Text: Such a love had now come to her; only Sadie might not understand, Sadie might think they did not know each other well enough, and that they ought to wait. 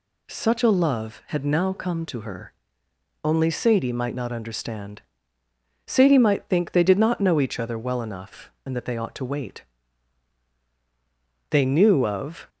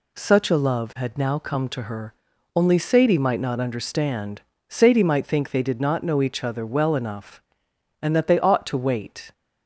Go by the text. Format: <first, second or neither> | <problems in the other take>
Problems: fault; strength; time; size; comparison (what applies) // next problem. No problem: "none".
second | goes on to say "They knew of"; noticeable; from 11.5 s on; 0.98 s long